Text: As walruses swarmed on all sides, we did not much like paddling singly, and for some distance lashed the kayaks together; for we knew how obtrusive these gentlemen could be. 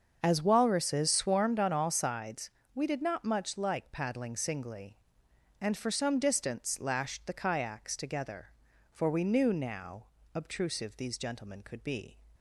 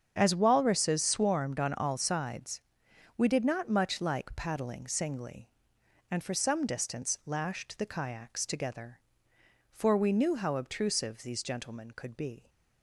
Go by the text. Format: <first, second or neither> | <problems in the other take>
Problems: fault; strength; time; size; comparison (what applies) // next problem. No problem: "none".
second | starts louder than the rest; until 1.2 s; 6.5 dB; strong in the second // says "now" for "how"; at 9.5 s